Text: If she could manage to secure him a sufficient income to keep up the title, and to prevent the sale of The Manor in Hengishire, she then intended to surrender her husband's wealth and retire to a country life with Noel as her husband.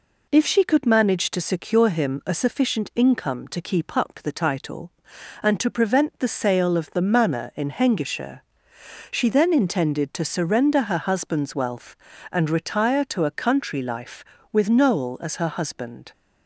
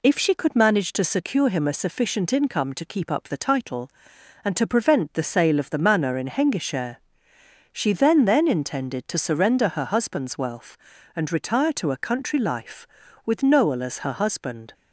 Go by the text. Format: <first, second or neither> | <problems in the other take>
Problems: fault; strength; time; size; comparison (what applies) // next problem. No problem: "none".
first | says "then" twice; at 8.2 s